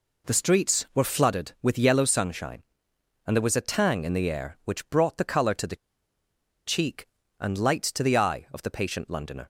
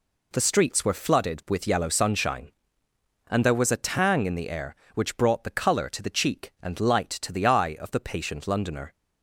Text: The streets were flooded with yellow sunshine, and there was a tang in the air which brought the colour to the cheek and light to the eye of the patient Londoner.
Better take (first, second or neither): second